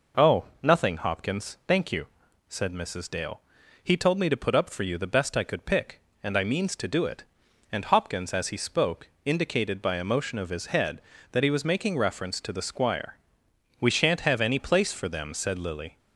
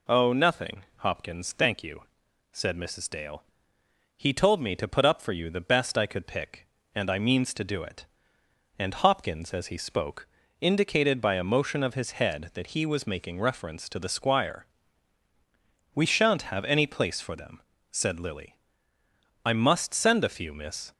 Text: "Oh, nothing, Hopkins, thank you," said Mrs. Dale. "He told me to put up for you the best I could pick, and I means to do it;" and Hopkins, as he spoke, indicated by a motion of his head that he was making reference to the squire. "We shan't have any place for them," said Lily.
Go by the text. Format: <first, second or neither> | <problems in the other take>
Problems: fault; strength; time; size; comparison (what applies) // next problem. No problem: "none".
first | goes on to say "I must send a few miss"; from 19.4 s on; 1.4 s long